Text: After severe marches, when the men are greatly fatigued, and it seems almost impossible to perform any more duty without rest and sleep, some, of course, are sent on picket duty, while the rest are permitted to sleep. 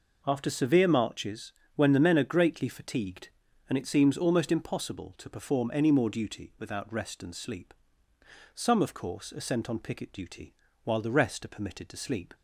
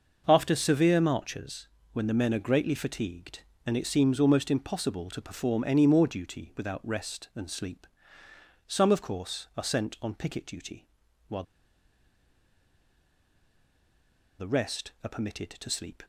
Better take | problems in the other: first | starts louder than the rest; noticeable; until 1.2 s; 6 dB // pauses between "while" and "the"; strong; at 11.4 s; 2.9 s long

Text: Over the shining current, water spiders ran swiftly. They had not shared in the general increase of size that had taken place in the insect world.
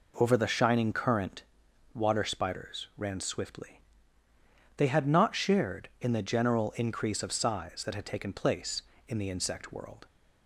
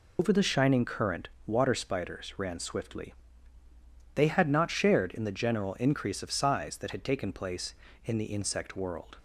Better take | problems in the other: first | loses the start of "Over"; at 0.1 s; 90 ms

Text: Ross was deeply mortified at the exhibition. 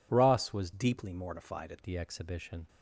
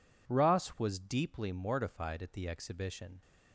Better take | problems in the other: second | changes voice from "deeply" to "at"; from 0.7 to 1.8 s; 1.1 s long

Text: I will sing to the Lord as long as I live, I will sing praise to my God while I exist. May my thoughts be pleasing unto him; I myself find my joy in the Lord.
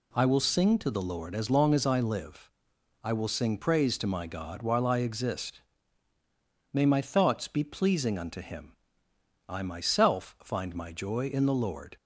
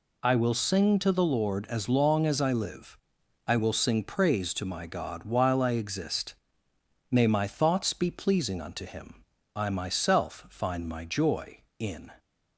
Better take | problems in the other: first | stops before "the Lord"; at 12.1 s

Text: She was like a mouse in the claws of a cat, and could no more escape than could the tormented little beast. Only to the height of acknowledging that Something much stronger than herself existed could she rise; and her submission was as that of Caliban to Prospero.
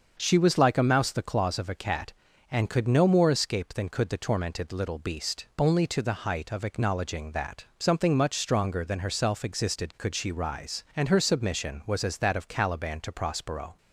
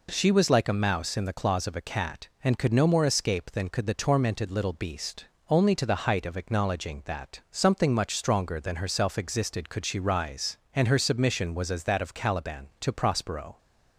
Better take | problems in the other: second | starts louder than the rest; until 1.2 s; 6.5 dB // skips "in"; at 1.1 s

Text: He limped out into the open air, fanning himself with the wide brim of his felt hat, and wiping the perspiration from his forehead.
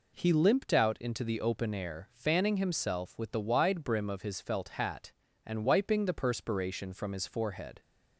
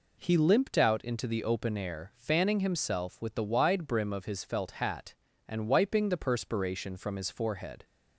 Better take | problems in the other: neither | none

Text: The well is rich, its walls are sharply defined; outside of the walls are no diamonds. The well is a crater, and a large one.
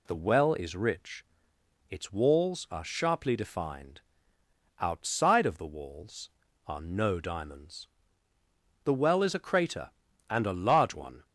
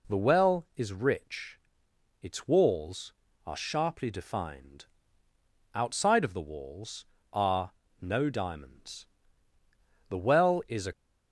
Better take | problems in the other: first | pauses between "are" and "no"; slight; at 7.7 s; 0.28 s long // stops before "crater and a large one"; at 10.9 s

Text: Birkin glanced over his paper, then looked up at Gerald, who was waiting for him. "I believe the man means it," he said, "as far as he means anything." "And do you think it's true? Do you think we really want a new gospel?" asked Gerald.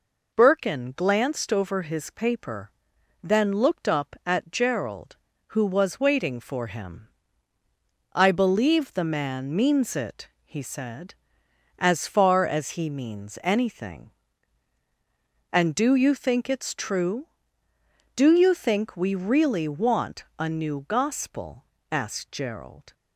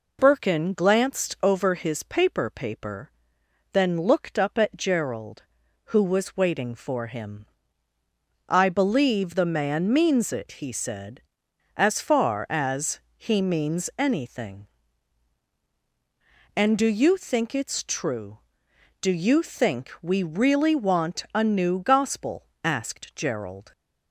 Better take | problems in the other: first | says "paper" twice; at 2.4 s // pauses between "as" and "he"; slight; at 12.9 s; 0.16 s long

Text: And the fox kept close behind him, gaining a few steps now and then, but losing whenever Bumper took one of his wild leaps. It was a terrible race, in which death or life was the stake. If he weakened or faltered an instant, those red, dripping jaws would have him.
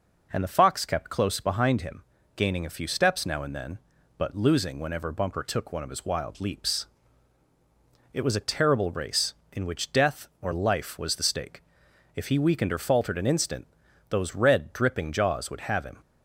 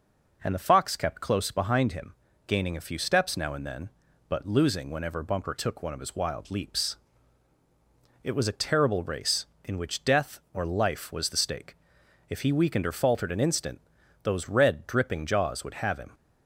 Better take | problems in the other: neither | none

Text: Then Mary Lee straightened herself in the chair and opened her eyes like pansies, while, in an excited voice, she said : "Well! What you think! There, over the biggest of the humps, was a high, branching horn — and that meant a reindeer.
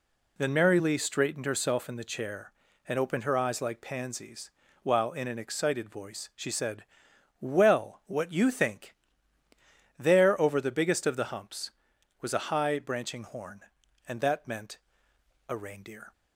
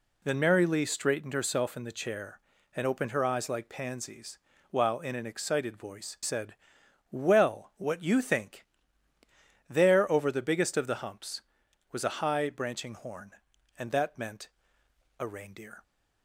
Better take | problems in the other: first | skips "she"; at 6.1 s // pauses between "meant" and "a"; noticeable; at 14.4 s; 0.70 s long; noticeable in the first

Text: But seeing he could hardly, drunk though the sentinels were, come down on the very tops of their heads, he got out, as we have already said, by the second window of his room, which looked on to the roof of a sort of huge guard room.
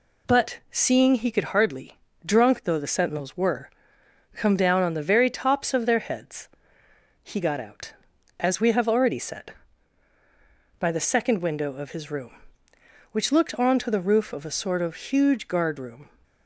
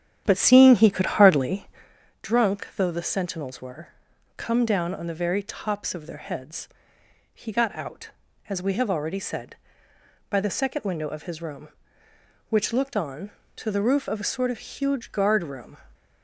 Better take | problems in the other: first | starts louder than the rest; strong; until 2.0 s; 10 dB

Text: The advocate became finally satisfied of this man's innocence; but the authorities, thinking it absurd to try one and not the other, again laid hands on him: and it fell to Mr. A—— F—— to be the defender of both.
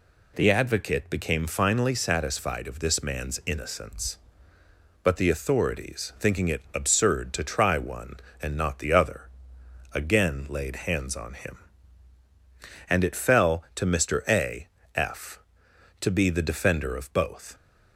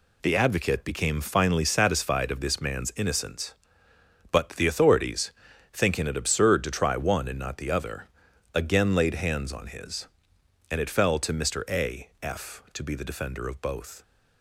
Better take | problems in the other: first | says "his" for "him"; at 9.6 s

